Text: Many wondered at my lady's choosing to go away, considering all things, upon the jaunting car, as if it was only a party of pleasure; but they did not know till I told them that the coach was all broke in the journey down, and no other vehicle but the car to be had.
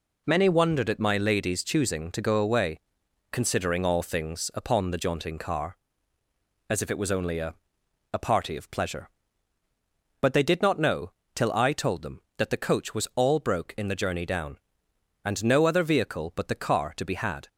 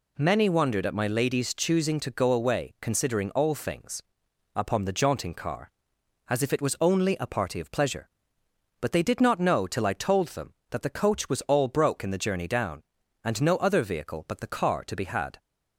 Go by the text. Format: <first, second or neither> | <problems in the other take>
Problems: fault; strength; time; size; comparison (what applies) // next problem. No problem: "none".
second | says "a" twice; at 8.1 s // pauses between "know" and "till"; slight; at 11.1 s; 0.22 s long